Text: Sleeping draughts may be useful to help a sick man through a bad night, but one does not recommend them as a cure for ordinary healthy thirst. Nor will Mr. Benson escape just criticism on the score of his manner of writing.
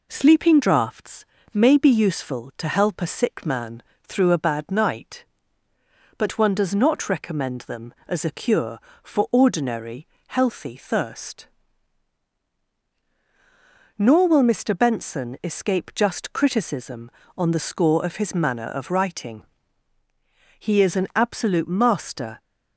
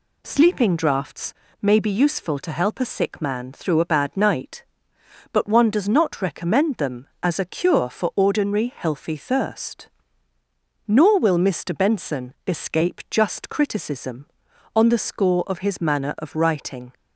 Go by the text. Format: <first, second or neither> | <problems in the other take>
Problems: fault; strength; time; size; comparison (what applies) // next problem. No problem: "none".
second | pauses between "draughts" and "may"; slight; at 1.2 s; 0.26 s long; slight in the second // pauses between "man" and "through"; slight; at 3.8 s; 0.20 s long // pauses between "ordinary" and "healthy"; slight; at 10.0 s; 0.22 s long // goes on to say "He is an absolute master"; strong; from 20.5 s on; 1.8 s long